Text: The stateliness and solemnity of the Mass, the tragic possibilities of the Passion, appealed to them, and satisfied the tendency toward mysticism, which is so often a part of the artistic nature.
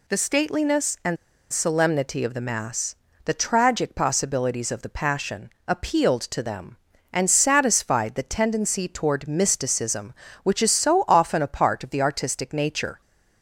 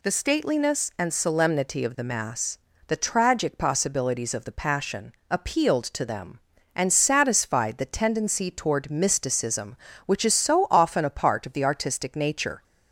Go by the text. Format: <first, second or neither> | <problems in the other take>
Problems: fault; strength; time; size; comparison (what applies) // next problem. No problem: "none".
second | pauses between "and" and "solemnity"; slight; at 1.1 s; 0.36 s long